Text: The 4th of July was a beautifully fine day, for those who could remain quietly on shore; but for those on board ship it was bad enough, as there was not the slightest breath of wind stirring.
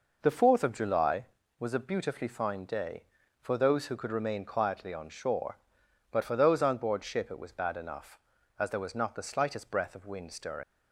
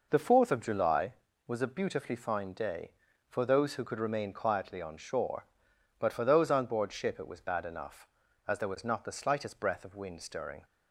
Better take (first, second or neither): second